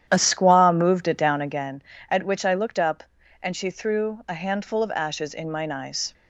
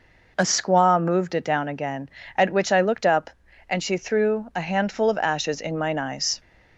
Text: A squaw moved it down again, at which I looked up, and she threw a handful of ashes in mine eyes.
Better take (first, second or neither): second